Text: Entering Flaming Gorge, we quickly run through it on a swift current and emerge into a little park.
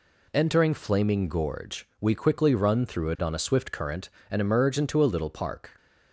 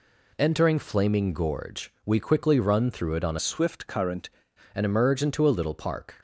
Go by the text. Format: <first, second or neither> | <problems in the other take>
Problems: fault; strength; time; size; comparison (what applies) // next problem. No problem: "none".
first | changes voice from "swift" to "current"; from 3.3 to 4.2 s; 0.9 s long